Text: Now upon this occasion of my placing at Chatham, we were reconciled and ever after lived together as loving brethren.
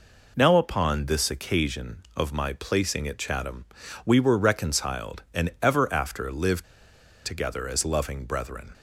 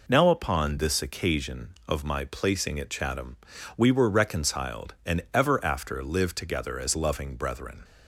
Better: second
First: pauses between "lived" and "together"; noticeable; at 6.6 s; 0.61 s long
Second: none

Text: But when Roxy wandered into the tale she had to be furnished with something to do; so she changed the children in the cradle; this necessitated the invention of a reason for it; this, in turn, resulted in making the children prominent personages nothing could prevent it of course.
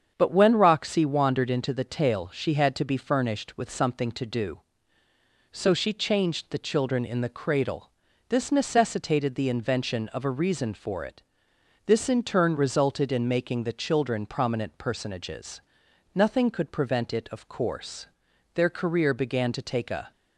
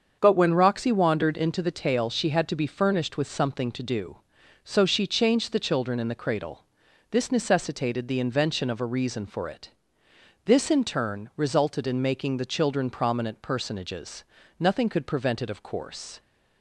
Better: second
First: starts louder than the rest; strong; until 1.1 s; 7.5 dB // pauses between "personages" and "nothing"; noticeable; at 15.6 s; 0.52 s long // goes on to say "Their career began to take a"; from 18.5 s on; 1.5 s long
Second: starts louder than the rest; until 1.2 s; 7 dB // pauses between "personages" and "nothing"; slight; at 14.2 s; 0.34 s long

